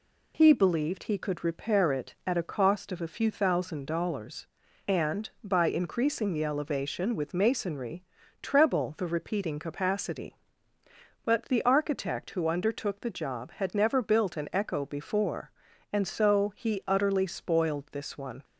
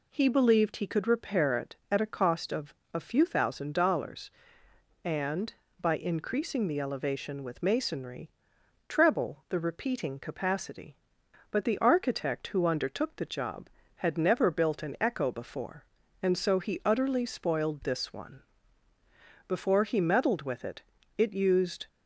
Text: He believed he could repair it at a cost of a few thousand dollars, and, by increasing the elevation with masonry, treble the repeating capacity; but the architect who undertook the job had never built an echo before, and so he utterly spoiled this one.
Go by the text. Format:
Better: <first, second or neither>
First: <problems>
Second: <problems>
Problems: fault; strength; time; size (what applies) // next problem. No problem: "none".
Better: first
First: none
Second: pauses between "of" and "a"; slight; at 2.7 s; 0.20 s long // goes on to say "Before he meddled with it it used"; strong; from 19.4 s on; 2.4 s long